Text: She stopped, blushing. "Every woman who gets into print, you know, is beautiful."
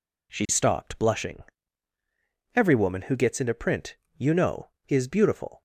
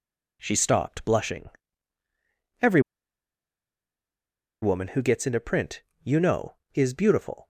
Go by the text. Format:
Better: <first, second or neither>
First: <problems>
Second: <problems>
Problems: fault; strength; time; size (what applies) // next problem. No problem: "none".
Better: first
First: none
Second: pauses between "Every" and "woman"; strong; at 2.7 s; 1.8 s long